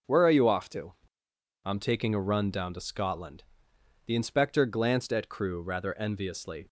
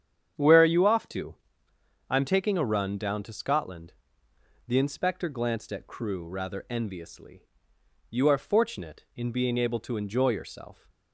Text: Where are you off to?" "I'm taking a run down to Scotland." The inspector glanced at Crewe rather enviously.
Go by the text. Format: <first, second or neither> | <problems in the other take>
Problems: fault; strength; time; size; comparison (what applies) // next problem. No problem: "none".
first | starts louder than the rest; strong; until 2.1 s; 8.5 dB; noticeable in the first // goes on to say "You are fortunate in being able to enjoy yourself"; strong; from 8.0 s on; 2.8 s long